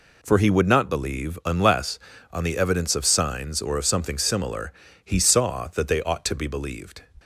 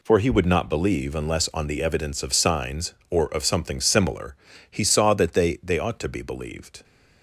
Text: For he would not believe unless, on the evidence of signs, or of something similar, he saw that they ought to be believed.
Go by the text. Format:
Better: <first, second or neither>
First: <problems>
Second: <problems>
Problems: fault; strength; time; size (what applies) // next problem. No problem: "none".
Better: first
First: none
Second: says "they" twice; at 5.6 s